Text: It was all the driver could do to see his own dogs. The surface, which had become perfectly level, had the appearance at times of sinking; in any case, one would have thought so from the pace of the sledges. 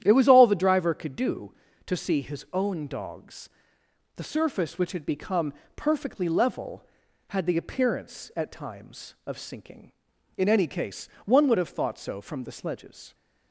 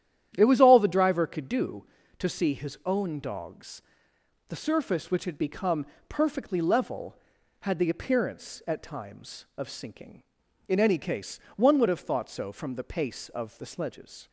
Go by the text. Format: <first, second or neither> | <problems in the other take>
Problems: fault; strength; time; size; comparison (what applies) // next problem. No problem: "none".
second | starts louder than the rest; strong; until 1.0 s; 11 dB; strong in the second // pauses between "become" and "perfectly"; slight; at 5.5 s; 0.22 s long; slight in the second // skips "the pace of"; at 12.4 s